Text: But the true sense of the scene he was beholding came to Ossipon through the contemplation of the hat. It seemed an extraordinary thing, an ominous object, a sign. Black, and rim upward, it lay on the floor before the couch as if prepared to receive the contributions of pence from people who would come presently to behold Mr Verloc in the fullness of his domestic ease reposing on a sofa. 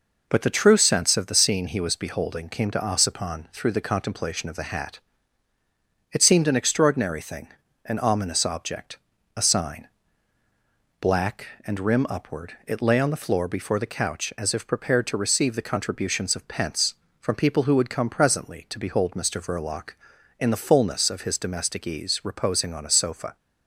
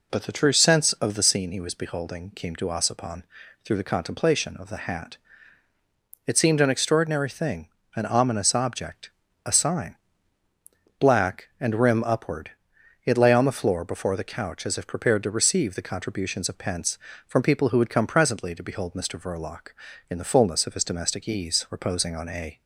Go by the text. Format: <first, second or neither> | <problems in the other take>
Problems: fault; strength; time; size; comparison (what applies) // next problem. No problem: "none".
first | pauses between "Ossipon" and "through"; at 3.2 s; 0.42 s long // stops before "sofa"; at 22.6 s